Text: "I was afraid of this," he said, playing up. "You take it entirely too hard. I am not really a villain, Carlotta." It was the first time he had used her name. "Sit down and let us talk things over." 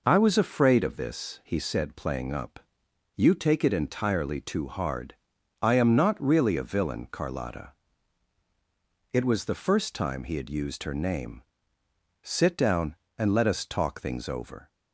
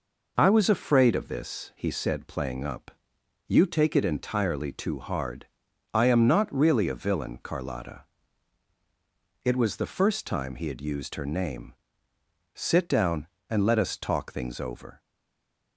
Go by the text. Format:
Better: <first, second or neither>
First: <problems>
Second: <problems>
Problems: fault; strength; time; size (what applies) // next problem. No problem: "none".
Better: first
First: none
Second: stays silent after the last word; slight; from 14.9 s on; 0.8 s long